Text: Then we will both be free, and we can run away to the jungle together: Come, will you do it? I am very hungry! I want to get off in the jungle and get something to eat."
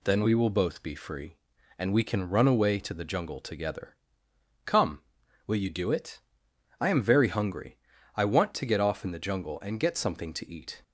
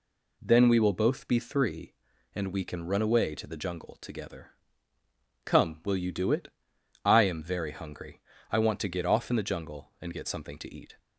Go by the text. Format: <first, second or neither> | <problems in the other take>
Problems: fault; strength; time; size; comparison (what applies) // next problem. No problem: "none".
first | says "three" for "free"; at 1.3 s